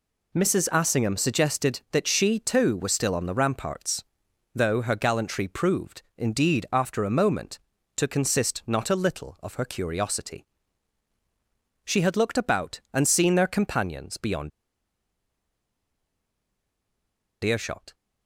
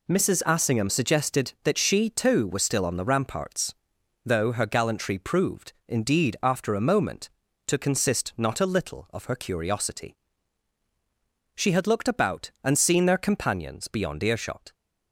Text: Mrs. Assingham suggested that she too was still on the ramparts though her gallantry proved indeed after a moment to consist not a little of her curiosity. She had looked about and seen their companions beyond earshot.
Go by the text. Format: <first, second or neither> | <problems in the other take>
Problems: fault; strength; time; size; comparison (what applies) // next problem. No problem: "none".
second | pauses between "ramparts" and "though"; noticeable; at 4.0 s; 0.52 s long; noticeable in the second // pauses between "beyond" and "earshot"; strong; at 14.5 s; 2.9 s long